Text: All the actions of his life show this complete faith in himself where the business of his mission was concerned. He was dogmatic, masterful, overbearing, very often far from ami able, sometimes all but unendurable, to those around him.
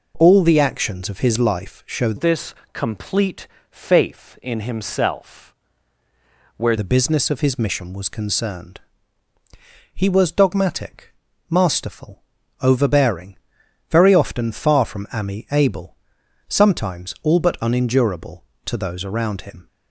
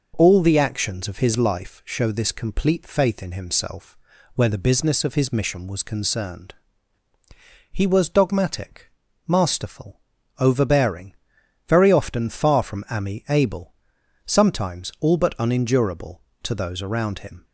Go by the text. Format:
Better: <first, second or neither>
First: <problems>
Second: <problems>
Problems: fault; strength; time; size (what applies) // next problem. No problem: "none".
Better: second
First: changes voice from "this" to "where"; from 2.1 to 6.7 s; 4.6 s long // pauses between "this" and "complete"; slight; at 2.5 s; 0.20 s long // pauses between "complete" and "faith"; slight; at 3.4 s; 0.24 s long // pauses between "himself" and "where"; at 5.5 s; 1.0 s long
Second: pauses between "himself" and "where"; at 3.9 s; 0.38 s long